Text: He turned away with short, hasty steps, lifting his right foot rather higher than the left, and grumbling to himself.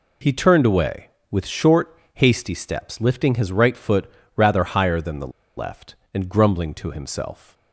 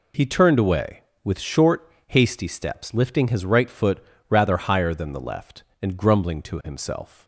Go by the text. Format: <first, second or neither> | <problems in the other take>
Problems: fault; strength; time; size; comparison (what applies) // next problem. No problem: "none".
second | pauses between "foot" and "rather"; slight; at 4.0 s; 0.28 s long; slight in the second // pauses between "the" and "left"; slight; at 5.3 s; 0.27 s long